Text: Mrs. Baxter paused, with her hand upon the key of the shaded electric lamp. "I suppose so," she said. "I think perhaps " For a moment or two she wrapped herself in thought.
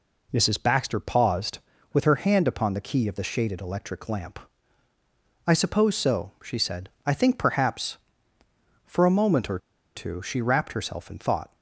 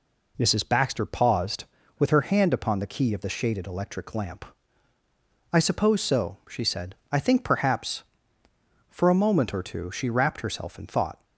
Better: second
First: pauses between "or" and "two"; at 9.5 s; 0.37 s long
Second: none

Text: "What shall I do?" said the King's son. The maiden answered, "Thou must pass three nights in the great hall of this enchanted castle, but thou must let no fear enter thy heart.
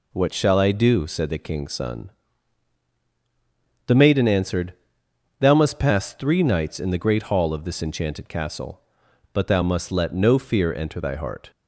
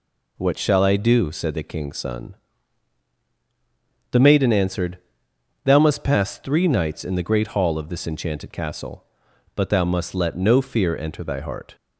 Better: neither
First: none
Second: none

